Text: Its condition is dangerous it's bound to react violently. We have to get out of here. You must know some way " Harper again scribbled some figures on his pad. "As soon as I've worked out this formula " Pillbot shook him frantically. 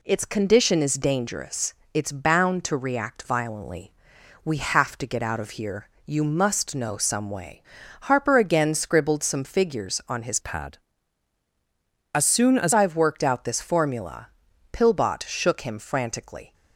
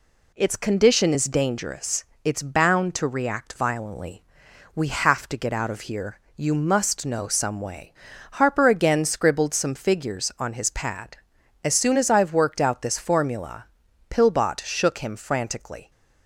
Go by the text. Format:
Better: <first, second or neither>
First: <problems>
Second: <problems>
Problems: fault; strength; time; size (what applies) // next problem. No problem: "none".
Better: second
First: pauses between "dangerous" and "it's"; slight; at 1.7 s; 0.20 s long // changes voice from "pad" to "as"; from 10.4 to 12.7 s; 2.3 s long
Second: pauses between "dangerous" and "it's"; slight; at 2.0 s; 0.20 s long